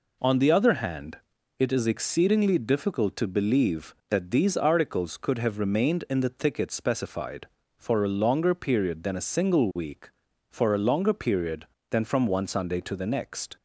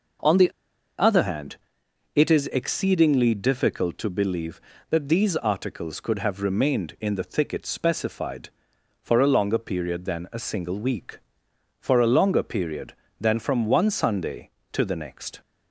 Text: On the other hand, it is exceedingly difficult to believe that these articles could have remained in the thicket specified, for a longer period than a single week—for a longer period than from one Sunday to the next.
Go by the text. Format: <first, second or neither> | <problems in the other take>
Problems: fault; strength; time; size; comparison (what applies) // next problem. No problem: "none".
first | pauses between "the" and "other"; noticeable; at 0.5 s; 0.48 s long